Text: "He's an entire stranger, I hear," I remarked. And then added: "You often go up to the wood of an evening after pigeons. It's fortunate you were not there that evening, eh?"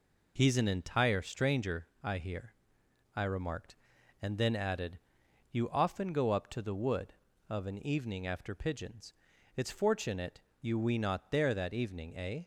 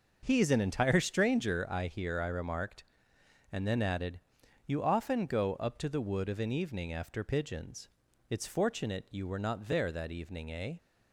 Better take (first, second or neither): second